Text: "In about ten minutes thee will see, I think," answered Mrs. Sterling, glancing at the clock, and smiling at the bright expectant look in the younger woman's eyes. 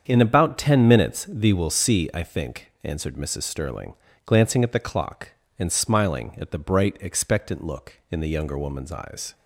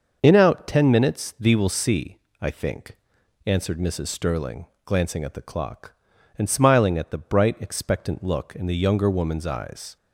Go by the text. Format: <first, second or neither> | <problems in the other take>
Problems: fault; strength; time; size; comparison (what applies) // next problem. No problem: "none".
first | starts louder than the rest; until 1.2 s; 6 dB; strong in the first // says "out" for "about"; at 0.3 s